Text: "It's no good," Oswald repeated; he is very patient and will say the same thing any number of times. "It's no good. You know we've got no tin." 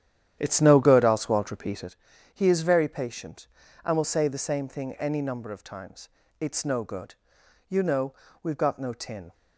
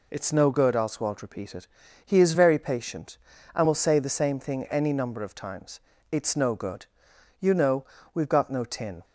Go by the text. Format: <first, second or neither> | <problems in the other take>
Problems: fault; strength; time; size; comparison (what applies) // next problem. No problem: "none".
second | starts louder than the rest; strong; until 1.9 s; 10.5 dB // pauses between "know" and "we've"; slight; at 8.1 s; 0.28 s long; slight in the second